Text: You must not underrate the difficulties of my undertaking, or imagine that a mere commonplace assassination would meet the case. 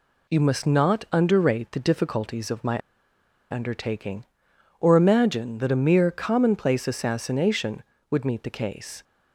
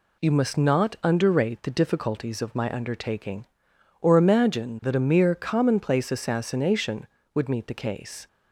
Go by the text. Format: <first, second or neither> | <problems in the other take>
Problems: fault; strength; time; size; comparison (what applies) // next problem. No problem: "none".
second | pauses between "my" and "undertaking"; noticeable; at 2.7 s; 0.76 s long